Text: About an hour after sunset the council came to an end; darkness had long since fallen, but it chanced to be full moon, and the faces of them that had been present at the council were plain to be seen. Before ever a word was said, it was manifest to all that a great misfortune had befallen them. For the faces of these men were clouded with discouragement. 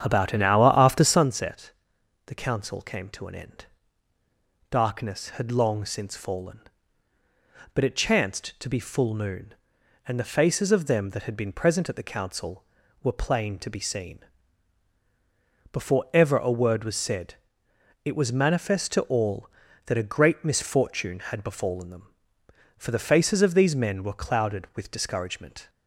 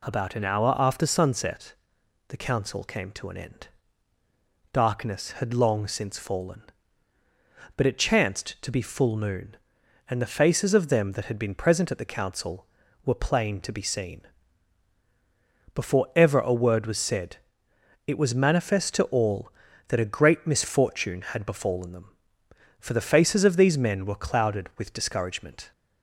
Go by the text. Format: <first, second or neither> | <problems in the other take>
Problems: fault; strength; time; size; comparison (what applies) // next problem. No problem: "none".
second | starts louder than the rest; strong; until 1.2 s; 8.5 dB // pauses between "sunset" and "the"; noticeable; at 1.7 s; 0.54 s long; noticeable in the second